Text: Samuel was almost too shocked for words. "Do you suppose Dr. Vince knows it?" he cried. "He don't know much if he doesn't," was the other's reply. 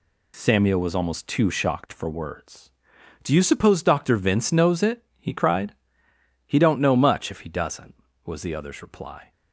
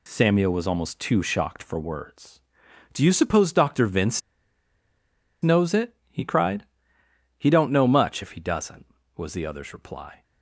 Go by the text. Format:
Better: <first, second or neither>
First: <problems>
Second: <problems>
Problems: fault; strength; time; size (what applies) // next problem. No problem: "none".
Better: first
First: none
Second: pauses between "Vince" and "knows"; at 4.2 s; 1.2 s long